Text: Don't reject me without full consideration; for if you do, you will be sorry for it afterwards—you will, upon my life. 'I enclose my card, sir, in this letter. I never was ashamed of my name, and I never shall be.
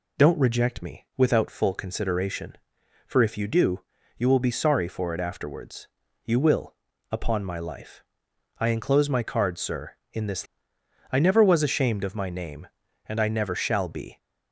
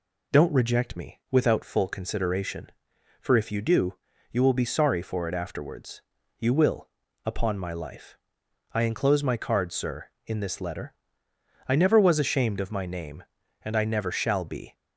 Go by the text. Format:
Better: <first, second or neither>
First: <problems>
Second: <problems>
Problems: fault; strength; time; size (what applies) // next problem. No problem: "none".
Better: second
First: skips "letter"; at 10.7 s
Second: none